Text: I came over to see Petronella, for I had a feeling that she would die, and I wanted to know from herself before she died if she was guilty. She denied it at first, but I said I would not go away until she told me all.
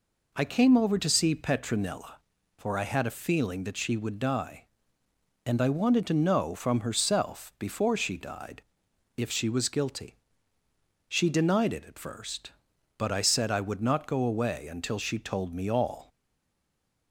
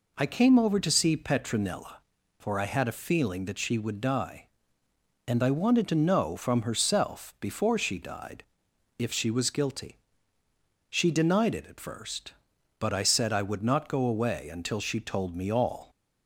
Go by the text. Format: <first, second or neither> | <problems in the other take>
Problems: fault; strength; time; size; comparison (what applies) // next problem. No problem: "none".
second | pauses between "died" and "if"; noticeable; at 8.6 s; 0.52 s long; noticeable in the second // stays silent after the last word; from 16.0 s on; 1.1 s long